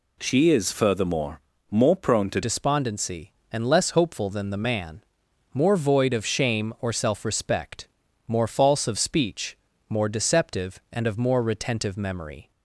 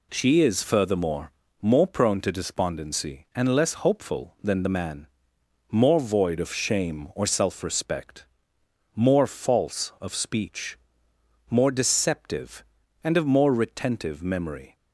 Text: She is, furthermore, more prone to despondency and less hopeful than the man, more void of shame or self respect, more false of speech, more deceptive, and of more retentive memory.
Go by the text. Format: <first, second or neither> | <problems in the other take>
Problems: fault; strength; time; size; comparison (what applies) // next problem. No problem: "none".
second | changes voice at "despondency"; from 2.4 s on; 10.1 s long